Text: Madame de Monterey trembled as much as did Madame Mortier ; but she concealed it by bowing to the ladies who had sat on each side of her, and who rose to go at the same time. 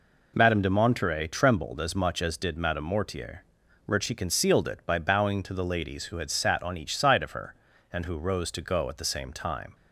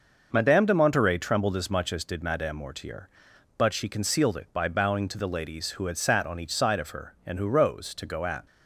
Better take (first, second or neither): first